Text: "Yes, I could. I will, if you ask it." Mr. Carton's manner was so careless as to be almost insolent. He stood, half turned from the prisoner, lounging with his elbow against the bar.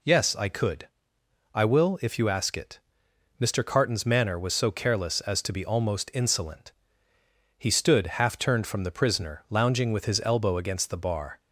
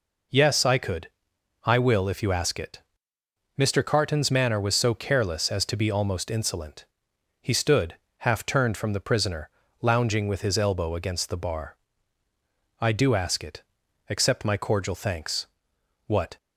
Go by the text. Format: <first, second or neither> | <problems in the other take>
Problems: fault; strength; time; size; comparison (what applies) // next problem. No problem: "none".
first | goes on to say "I do ask it Accept my cordial thanks What"; strong; from 12.7 s on; 3.5 s long